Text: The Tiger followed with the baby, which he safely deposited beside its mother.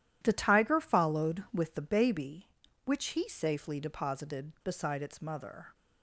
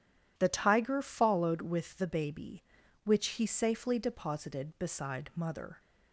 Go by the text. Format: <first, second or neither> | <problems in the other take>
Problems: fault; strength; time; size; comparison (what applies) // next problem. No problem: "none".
first | skips "its"; at 5.3 s